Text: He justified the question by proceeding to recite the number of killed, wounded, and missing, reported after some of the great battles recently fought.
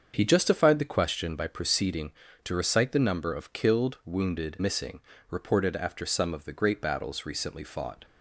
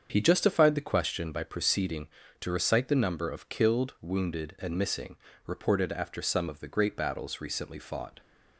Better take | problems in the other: second | starts louder than the rest; until 1.1 s; 7 dB; strong in the second // skips "and"; at 4.6 s

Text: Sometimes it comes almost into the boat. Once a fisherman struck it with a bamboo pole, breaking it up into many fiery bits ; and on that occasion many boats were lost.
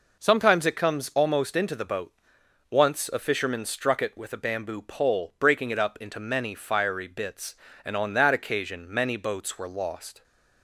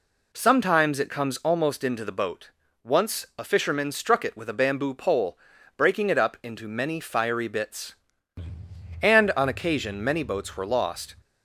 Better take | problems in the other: first | skips "that"; at 9.4 s

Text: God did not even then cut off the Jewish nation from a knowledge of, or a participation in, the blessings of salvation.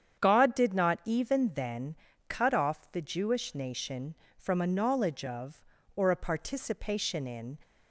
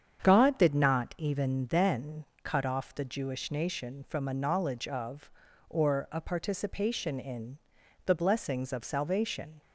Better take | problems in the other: second | starts louder than the rest; strong; until 1.2 s; 8.5 dB; strong in the second // pauses between "then" and "cut"; slight; at 1.9 s; 0.32 s long; slight in the second // stops before "the blessings of salvation"; at 7.6 s

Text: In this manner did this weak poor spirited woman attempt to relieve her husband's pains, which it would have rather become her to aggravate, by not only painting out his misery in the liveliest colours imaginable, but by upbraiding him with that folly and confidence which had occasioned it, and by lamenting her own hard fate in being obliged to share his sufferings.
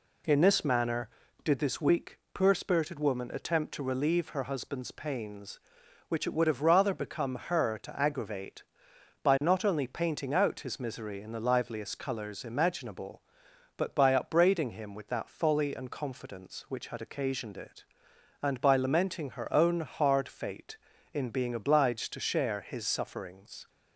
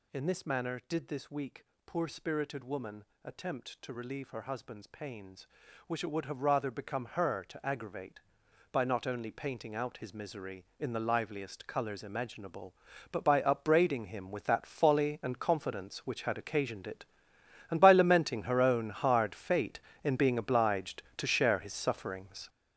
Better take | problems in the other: first | gets louder; strong; throughout; 9.5 dB // pauses between "weak" and "poor"; slight; at 1.6 s; 0.22 s long; slight in the first // pauses between "woman" and "attempt"; slight; at 3.0 s; 0.20 s long

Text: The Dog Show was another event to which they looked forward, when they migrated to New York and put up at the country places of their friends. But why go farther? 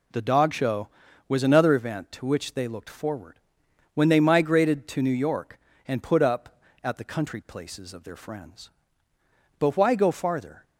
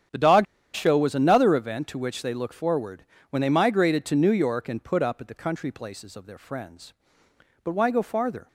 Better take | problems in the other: first | starts louder than the rest; strong; until 1.4 s; 9 dB // pauses between "Dog" and "Show"; slight; at 0.4 s; 0.29 s long

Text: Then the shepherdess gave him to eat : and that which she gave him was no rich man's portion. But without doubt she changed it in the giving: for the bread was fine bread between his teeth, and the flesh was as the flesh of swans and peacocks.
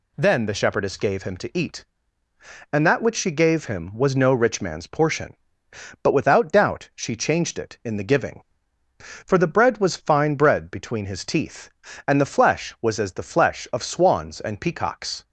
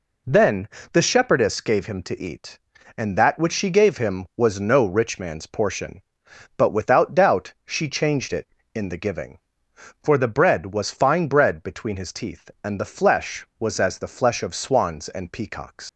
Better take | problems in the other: first | pauses between "Then" and "the"; slight; at 0.6 s; 0.24 s long // leaves "peacocks" unfinished; at 15.8 s; 100 ms

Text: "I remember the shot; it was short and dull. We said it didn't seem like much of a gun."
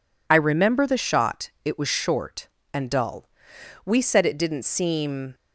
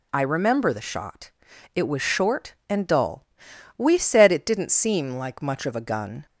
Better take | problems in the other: second | stops before "like much of a gun"; at 5.3 s

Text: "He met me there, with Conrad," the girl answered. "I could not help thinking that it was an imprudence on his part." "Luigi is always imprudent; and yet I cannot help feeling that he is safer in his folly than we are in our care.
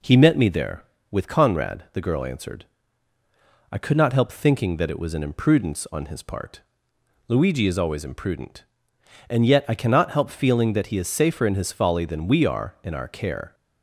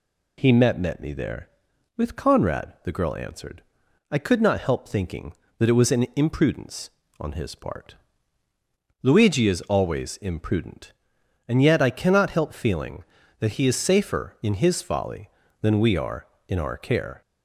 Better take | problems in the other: first | says "met" twice; at 0.7 s

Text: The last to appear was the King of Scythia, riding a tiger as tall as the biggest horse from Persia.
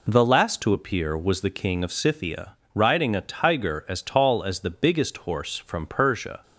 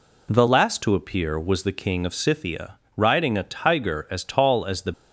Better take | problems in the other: first | stops before "biggest horse from Persia"; at 4.9 s

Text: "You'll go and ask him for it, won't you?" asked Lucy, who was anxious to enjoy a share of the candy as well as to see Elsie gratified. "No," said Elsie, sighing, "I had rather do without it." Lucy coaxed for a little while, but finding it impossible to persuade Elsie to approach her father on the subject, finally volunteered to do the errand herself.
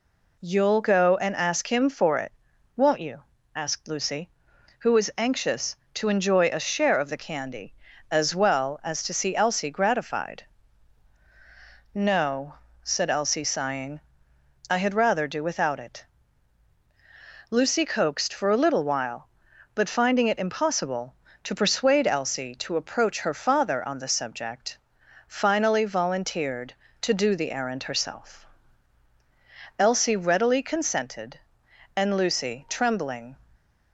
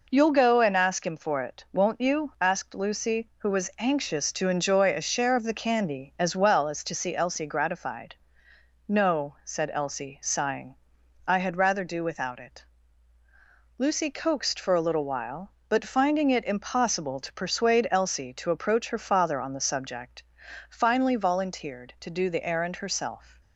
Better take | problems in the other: second | goes on to say "Elsie readily consented and Lucy trembling"; strong; from 29.7 s on; 3.5 s long

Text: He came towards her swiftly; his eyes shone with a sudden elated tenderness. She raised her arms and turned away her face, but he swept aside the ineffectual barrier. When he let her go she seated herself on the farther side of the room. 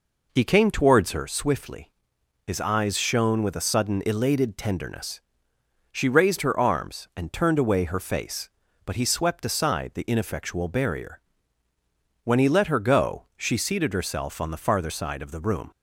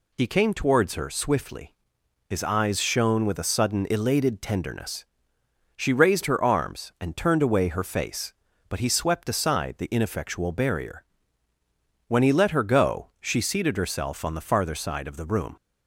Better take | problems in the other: second | starts louder than the rest; noticeable; until 1.3 s; 4.5 dB

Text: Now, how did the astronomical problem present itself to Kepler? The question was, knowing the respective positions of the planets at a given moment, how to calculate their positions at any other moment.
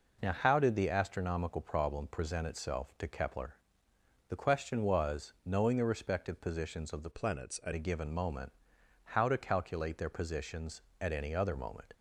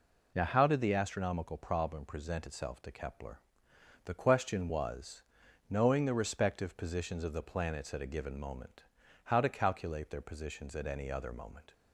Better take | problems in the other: second | changes voice from "planets" to "at"; from 7.1 to 7.7 s; 0.6 s long

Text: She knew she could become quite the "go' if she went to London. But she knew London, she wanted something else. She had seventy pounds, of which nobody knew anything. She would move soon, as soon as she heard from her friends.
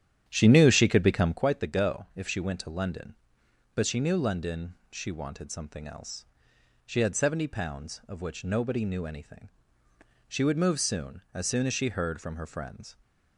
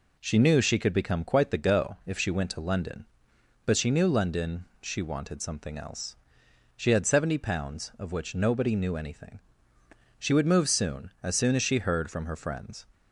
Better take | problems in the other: second | starts louder than the rest; strong; until 1.4 s; 10.5 dB

